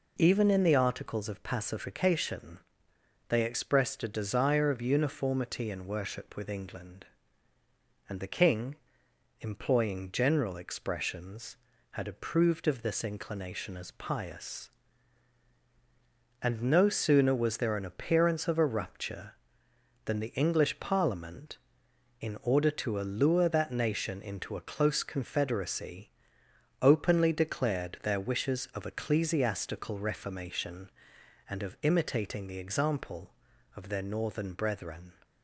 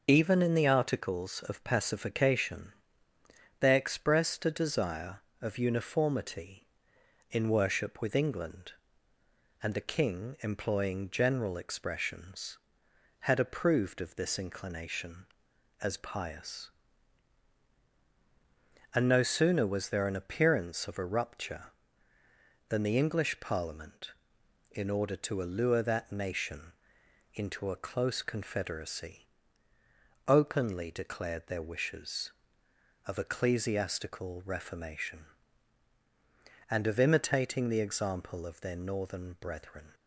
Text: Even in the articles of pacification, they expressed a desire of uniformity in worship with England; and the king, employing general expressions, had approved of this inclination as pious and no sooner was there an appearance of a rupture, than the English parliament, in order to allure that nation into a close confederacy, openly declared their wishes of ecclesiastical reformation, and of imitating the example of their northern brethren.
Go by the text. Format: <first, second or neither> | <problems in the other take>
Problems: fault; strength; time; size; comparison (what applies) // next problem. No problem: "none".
first | loses the start of "Even"; at 0.0 s; 45 ms // pauses between "nation" and "into"; noticeable; at 26.7 s; 0.64 s long